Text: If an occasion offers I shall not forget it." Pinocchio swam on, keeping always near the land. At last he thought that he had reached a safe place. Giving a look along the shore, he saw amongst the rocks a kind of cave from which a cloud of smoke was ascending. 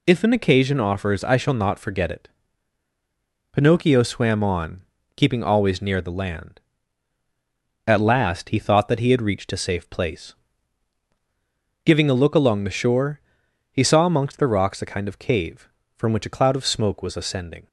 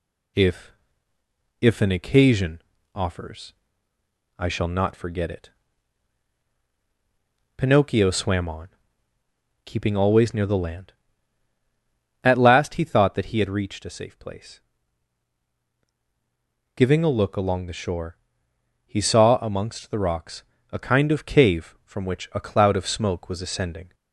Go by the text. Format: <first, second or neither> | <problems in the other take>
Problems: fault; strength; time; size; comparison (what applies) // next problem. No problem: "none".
first | says "If" twice; at 1.5 s // pauses between "occasion" and "offers"; slight; at 2.5 s; 0.32 s long // pauses between "offers" and "I"; noticeable; at 3.5 s; 0.82 s long // pauses between "rocks" and "a"; slight; at 20.4 s; 0.30 s long